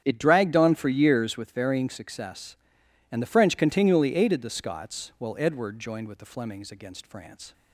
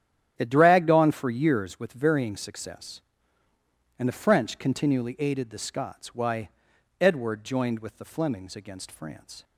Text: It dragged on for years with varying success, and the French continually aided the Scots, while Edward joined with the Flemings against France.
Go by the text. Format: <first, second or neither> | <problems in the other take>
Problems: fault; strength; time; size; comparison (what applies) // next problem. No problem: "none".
first | starts louder than the rest; strong; until 1.3 s; 10.5 dB; strong in the first // says "why" for "while"; at 6.1 s